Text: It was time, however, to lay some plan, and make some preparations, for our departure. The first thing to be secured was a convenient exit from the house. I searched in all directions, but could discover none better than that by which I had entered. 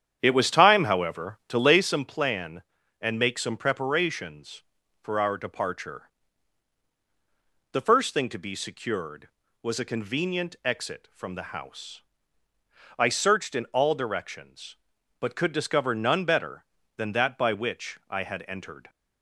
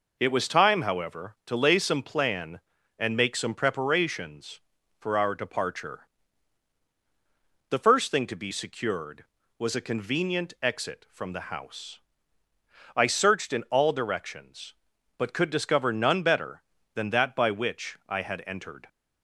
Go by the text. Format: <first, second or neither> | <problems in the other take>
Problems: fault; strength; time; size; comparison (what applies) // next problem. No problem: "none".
second | starts louder than the rest; strong; until 1.8 s; 9 dB